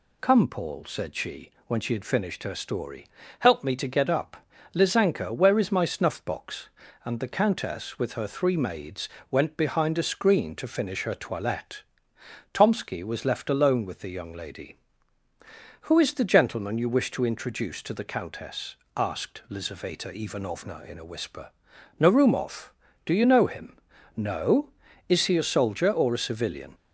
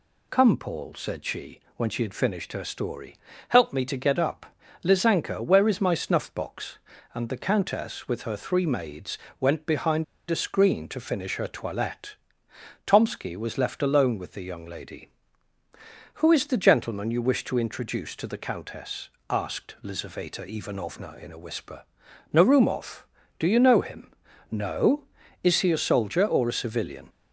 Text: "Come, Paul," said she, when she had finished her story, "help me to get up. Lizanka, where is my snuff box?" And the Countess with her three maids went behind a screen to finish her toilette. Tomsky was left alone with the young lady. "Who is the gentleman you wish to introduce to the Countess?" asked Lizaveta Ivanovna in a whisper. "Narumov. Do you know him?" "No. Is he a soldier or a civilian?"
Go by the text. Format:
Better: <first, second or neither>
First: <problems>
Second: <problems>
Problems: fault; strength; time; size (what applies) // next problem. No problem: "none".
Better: first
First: pauses between "maids" and "went"; slight; at 9.0 s; 0.22 s long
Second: pauses between "maids" and "went"; slight; at 9.1 s; 0.22 s long // pauses between "behind" and "a"; slight; at 10.0 s; 0.24 s long